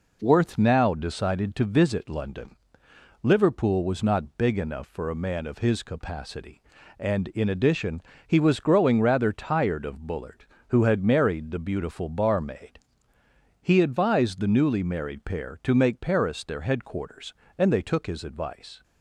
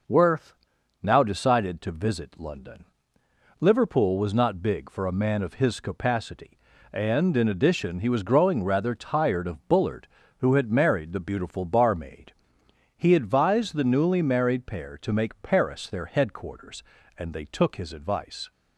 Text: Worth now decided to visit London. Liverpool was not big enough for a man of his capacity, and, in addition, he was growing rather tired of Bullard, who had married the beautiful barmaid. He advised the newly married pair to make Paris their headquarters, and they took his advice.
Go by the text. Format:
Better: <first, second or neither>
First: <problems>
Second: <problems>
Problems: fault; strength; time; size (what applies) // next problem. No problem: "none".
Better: first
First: none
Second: pauses between "Worth" and "now"; noticeable; at 0.5 s; 0.48 s long // skips "enough"; at 4.9 s